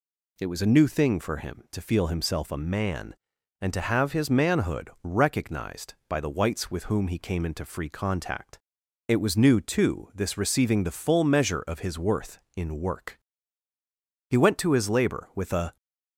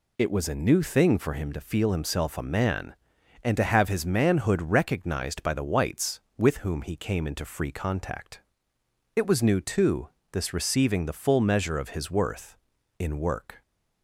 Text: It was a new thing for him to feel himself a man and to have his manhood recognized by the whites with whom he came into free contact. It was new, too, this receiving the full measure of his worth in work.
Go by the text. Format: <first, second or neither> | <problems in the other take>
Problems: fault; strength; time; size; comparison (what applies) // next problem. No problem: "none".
second | goes on to say "He went to his labor with a"; from 14.2 s on; 1.4 s long